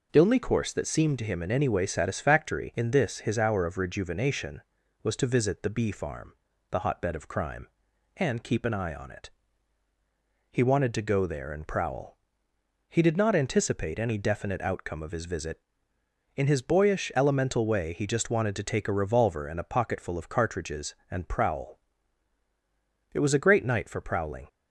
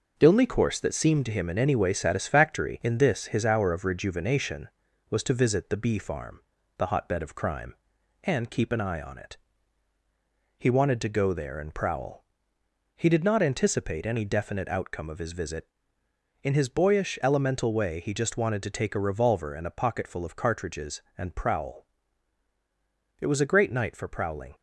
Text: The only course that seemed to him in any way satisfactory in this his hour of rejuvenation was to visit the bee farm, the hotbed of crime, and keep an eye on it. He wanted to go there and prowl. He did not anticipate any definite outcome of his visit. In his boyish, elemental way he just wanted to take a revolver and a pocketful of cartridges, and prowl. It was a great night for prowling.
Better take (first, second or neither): first